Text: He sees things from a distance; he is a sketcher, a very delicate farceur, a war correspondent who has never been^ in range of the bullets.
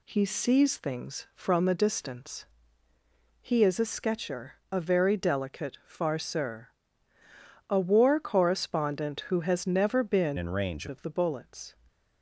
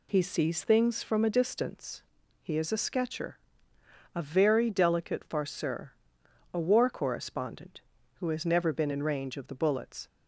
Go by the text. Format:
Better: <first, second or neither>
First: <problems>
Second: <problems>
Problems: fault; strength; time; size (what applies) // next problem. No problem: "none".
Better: second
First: changes voice from "in" to "range"; from 10.3 to 10.8 s; 0.5 s long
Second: none